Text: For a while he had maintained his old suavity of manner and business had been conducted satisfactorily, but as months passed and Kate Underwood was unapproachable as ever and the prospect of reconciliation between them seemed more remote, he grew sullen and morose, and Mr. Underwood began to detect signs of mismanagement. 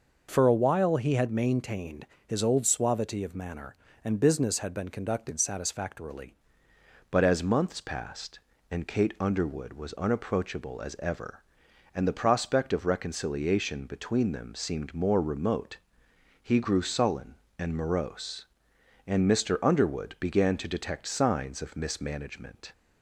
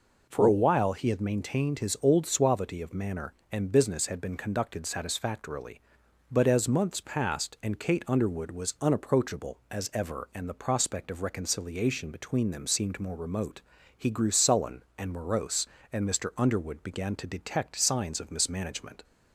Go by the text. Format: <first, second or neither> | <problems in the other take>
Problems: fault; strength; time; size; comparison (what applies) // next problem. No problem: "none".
second | pauses between "maintained" and "his"; slight; at 2.0 s; 0.22 s long // changes voice at "but"; from 7.1 s on; 15.6 s long